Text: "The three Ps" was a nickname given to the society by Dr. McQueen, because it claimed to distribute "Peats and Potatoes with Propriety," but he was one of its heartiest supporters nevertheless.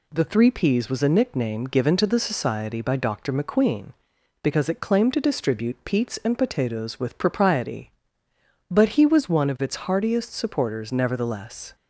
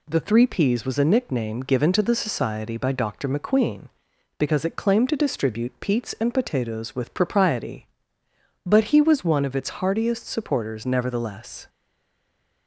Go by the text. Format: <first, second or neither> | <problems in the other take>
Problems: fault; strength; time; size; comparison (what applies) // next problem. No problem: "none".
first | stays silent after the last word; from 11.6 s on; 1.0 s long